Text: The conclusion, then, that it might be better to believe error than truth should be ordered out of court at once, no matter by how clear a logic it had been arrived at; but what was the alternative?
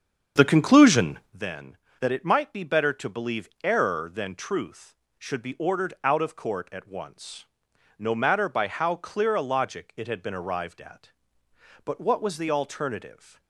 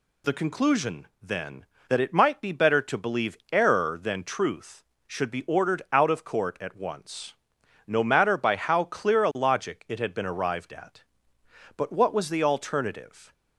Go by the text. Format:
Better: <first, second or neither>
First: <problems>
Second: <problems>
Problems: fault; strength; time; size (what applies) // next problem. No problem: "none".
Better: second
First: starts louder than the rest; strong; until 1.4 s; 7.5 dB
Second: none